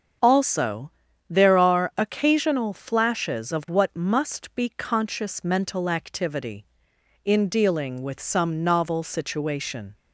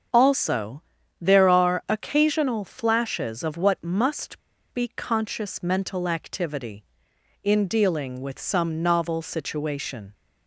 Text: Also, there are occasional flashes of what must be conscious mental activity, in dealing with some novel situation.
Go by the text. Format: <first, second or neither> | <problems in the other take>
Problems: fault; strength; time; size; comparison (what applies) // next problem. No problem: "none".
first | starts louder than the rest; strong; until 1.5 s; 7 dB; strong in the first // pauses between "must" and "be"; slight; at 4.3 s; 0.32 s long